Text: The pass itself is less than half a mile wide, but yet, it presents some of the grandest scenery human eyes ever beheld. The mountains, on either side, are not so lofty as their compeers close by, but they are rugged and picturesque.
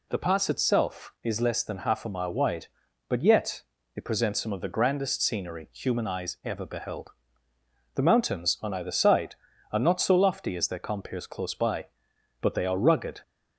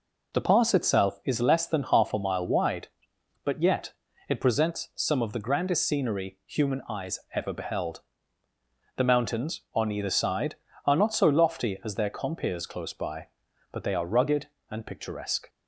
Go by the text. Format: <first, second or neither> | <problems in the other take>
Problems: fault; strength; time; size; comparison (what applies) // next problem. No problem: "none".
second | stops before "and picturesque"; at 13.2 s